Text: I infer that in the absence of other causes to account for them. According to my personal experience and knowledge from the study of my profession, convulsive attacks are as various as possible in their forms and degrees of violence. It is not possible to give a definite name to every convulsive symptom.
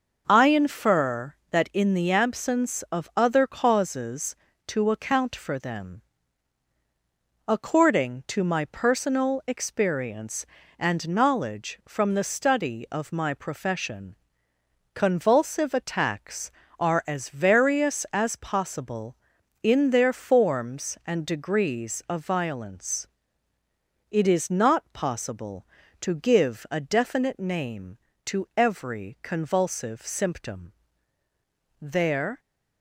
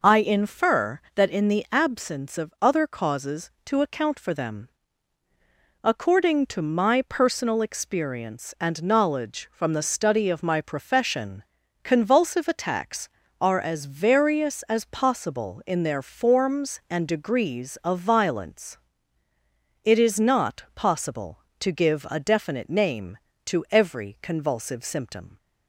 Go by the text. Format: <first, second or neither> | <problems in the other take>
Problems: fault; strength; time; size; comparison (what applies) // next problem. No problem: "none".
second | goes on to say "There"; from 31.7 s on; 0.60 s long